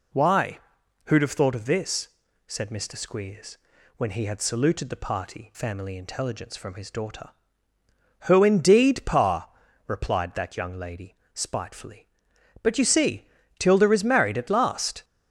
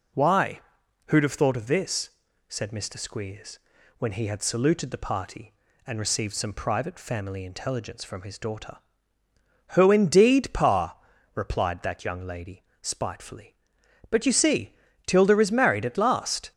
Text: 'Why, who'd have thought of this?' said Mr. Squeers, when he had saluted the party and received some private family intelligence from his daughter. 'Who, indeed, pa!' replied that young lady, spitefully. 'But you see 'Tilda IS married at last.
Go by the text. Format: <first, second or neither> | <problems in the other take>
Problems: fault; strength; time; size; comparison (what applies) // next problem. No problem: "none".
second | skips "and received some private"; at 5.5 s // pauses between "see" and "Tilda"; slight; at 13.2 s; 0.30 s long; slight in the second